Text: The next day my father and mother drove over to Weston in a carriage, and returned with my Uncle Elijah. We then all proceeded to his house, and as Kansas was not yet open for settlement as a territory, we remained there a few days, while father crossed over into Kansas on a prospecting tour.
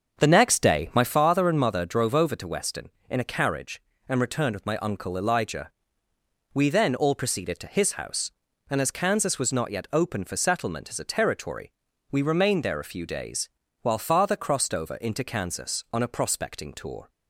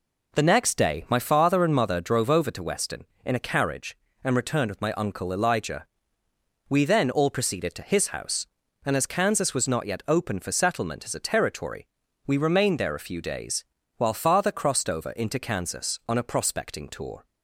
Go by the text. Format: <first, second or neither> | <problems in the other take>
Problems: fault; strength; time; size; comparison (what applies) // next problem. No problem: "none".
second | starts louder than the rest; until 1.2 s; 7 dB